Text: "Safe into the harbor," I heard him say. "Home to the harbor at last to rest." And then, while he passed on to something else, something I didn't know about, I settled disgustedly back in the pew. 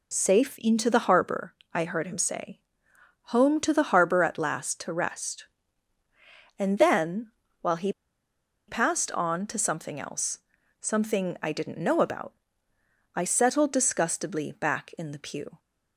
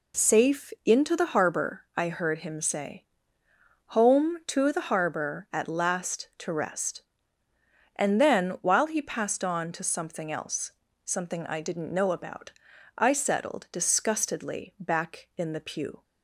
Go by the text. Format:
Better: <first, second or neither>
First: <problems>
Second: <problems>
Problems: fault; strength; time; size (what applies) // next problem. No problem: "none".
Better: second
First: pauses between "he" and "passed"; noticeable; at 7.9 s; 0.75 s long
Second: none